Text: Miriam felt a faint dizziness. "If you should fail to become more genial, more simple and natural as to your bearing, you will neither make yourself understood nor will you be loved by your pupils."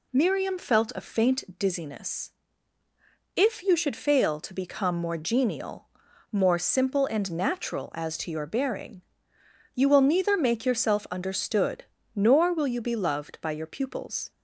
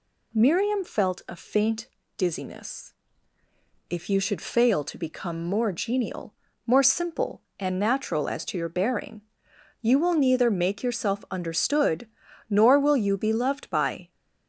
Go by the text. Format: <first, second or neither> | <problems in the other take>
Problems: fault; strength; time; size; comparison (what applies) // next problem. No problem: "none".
first | pauses between "faint" and "dizziness"; slight; at 1.8 s; 0.28 s long // pauses between "understood" and "nor"; at 12.0 s; 0.42 s long; slight in the first // stops before "your pupils"; at 14.1 s